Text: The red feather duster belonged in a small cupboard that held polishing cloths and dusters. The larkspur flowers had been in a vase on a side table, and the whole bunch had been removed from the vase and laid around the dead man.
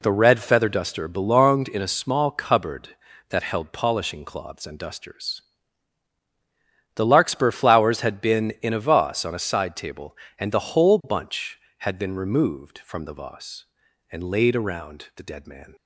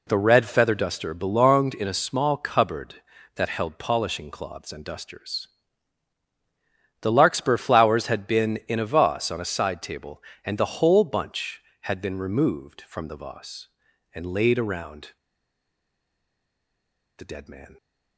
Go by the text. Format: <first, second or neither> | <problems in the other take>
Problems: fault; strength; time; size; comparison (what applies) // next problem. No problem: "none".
first | pauses between "around" and "the"; strong; at 15.0 s; 2.0 s long